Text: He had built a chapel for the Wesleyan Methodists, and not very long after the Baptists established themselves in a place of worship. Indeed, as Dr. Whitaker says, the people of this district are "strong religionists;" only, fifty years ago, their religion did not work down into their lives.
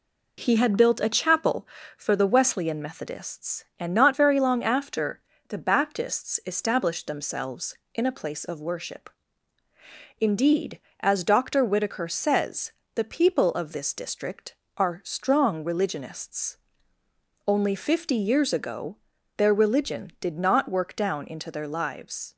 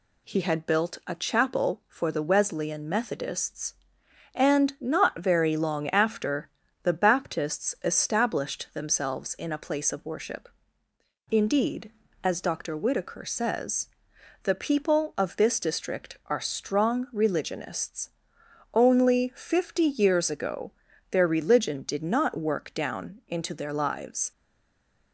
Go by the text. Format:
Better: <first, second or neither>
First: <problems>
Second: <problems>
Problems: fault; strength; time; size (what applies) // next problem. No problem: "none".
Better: first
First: pauses between "after" and "the"; slight; at 5.1 s; 0.30 s long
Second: pauses between "after" and "the"; slight; at 6.4 s; 0.32 s long // stays silent after the last word; slight; from 24.3 s on; 0.8 s long